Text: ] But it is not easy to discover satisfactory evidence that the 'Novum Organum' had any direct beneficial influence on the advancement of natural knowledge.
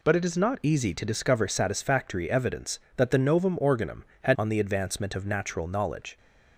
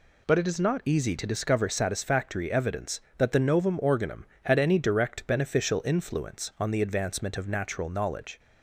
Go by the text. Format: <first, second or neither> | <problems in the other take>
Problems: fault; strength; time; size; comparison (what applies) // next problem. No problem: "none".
second | skips "any direct beneficial influence"; at 4.3 s